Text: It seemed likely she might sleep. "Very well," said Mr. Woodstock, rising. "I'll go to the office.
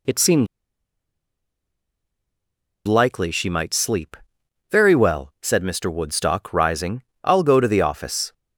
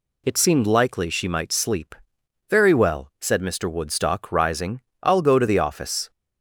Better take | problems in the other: second | pauses between "seemed" and "likely"; strong; at 0.4 s; 2.4 s long

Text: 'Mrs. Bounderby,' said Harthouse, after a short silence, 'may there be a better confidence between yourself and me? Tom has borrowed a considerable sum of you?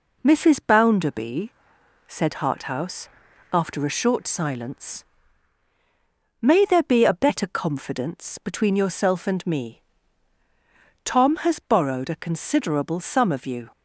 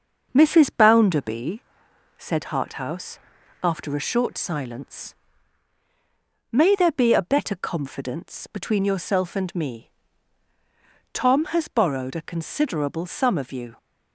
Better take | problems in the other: first | starts louder than the rest; until 1.6 s; 6 dB

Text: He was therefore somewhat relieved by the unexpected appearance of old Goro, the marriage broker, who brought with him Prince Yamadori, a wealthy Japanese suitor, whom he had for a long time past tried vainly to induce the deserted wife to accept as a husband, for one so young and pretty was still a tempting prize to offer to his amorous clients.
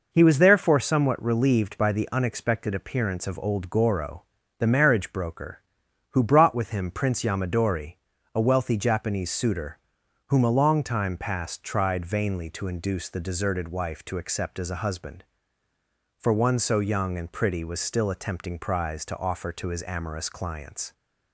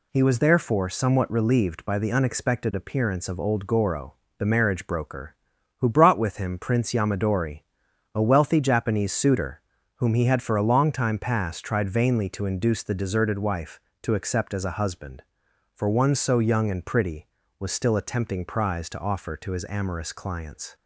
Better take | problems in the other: second | skips "he had for"; at 10.4 s

